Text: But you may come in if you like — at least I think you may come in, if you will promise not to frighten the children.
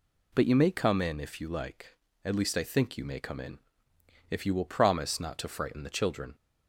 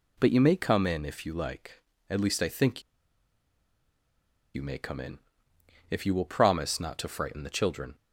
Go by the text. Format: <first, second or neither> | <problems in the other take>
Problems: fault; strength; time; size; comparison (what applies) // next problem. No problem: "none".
first | pauses between "think" and "you"; strong; at 2.8 s; 1.7 s long